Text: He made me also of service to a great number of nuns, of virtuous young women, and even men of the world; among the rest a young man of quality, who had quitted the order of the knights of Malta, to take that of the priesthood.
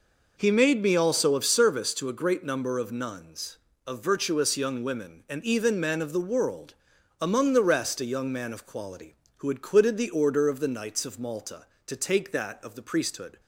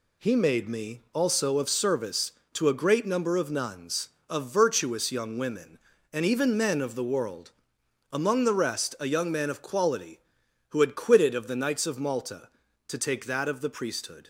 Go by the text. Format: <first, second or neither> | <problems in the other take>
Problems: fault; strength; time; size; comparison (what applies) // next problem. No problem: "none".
first | skips "the order"; at 11.3 s